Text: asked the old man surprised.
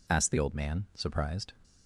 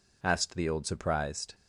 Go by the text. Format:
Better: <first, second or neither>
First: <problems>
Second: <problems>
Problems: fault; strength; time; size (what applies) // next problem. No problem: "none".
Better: first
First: none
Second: skips "man"; at 0.8 s